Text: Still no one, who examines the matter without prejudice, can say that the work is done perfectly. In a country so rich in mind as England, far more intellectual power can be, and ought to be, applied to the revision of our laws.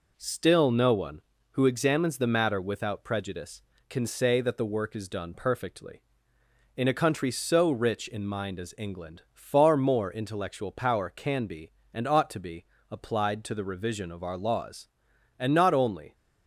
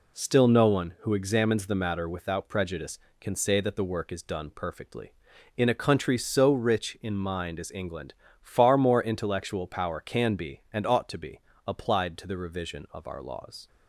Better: second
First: goes on to say "And not only"; noticeable; from 15.3 s on; 0.76 s long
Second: none

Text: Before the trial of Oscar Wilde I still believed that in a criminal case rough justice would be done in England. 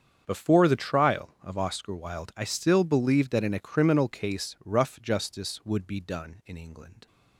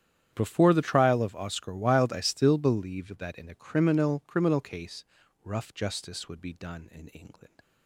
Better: first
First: starts louder than the rest; strong; until 1.2 s; 7.5 dB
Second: starts louder than the rest; strong; until 1.3 s; 9.5 dB // says "criminal" twice; at 4.2 s // pauses between "case" and "rough"; at 5.0 s; 0.40 s long

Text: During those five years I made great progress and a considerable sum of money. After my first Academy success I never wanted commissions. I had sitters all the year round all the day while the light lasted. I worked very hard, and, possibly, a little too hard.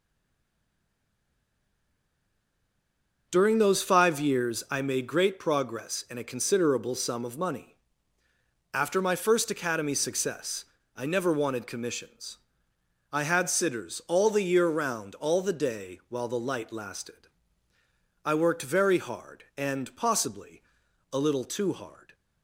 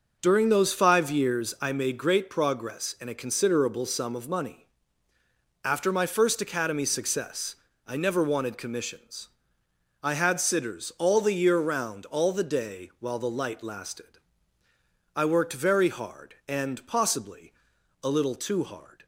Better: second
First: stays silent before the first word; strong; until 3.3 s; 3.3 s long // pauses between "success" and "I"; slight; at 10.6 s; 0.30 s long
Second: pauses between "success" and "I"; slight; at 7.5 s; 0.30 s long

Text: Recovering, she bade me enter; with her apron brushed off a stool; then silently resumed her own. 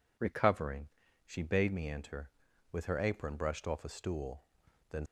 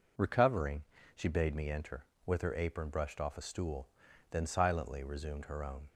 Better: second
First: stops before "silently resumed her own"; at 5.0 s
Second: none

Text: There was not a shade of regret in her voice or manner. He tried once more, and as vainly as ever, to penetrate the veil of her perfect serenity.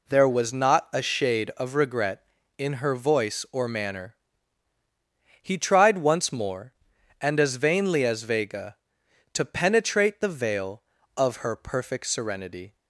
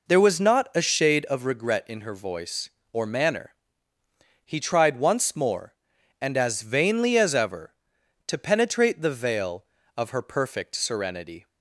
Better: second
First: says "vega" for "ever"; at 8.2 s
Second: none

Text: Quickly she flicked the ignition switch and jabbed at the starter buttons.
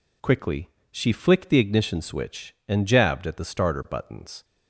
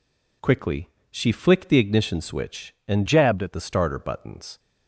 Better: first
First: pauses between "Quickly" and "she"; slight; at 0.6 s; 0.22 s long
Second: pauses between "Quickly" and "she"; slight; at 0.8 s; 0.22 s long // changes voice from "jabbed" to "at"; from 3.0 to 3.5 s; 0.5 s long

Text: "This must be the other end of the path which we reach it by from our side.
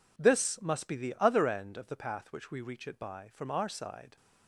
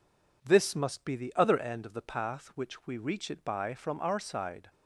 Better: neither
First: none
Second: none

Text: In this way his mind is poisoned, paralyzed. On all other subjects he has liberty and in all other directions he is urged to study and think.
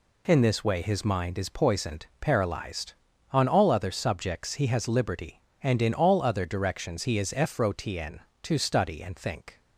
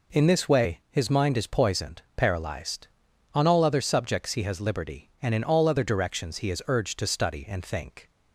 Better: second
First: says "frotn" for "urged"; at 7.3 s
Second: none

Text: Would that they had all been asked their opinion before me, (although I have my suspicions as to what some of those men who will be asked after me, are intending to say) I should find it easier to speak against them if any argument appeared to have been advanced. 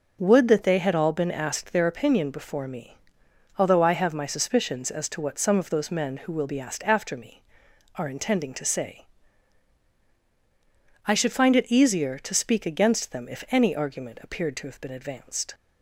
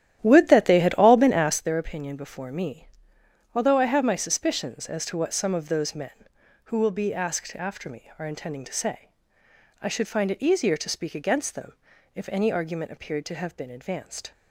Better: first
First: none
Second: starts louder than the rest; strong; until 1.7 s; 11.5 dB // pauses between "them" and "if"; at 11.7 s; 0.42 s long

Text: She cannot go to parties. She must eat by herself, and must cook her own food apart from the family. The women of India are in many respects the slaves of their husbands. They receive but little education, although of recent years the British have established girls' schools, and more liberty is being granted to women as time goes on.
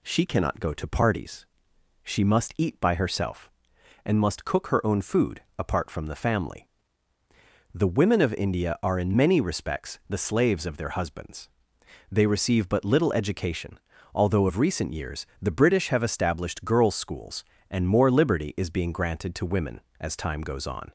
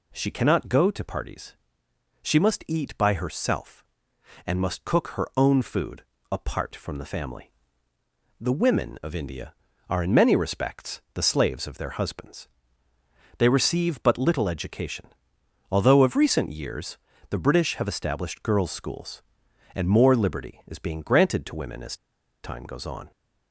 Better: first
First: pauses between "food" and "apart"; slight; at 5.3 s; 0.18 s long // pauses between "years" and "the"; slight; at 15.2 s; 0.16 s long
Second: pauses between "food" and "apart"; slight; at 6.0 s; 0.26 s long // pauses between "years" and "the"; slight; at 16.9 s; 0.32 s long // pauses between "as" and "time"; noticeable; at 21.9 s; 0.48 s long

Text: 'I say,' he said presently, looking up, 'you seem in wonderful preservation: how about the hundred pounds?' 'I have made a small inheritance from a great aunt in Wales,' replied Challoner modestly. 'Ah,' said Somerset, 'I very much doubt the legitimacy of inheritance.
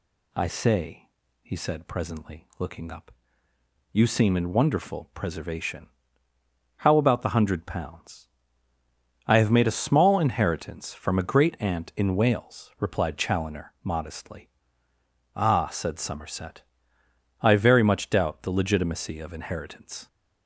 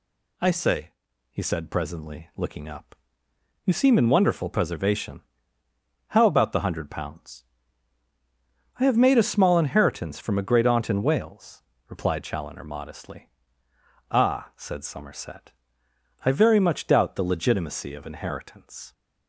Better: neither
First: none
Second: none

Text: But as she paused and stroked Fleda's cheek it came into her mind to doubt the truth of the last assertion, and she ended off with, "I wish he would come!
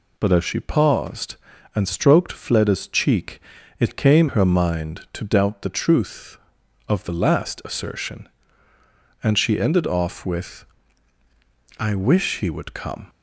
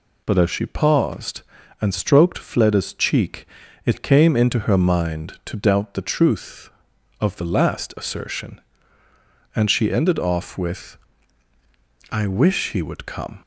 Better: second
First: pauses between "cheek" and "it"; at 3.3 s; 0.40 s long // skips "into"; at 4.2 s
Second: pauses between "cheek" and "it"; at 3.4 s; 0.40 s long

